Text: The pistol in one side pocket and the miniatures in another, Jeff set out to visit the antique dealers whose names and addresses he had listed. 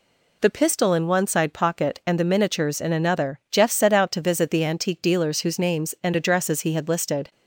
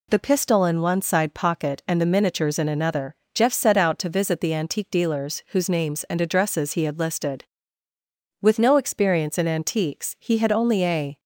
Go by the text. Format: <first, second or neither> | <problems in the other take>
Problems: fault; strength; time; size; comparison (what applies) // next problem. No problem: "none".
first | goes on to say "With no experience in antiques he had only a"; strong; from 8.4 s on; 2.7 s long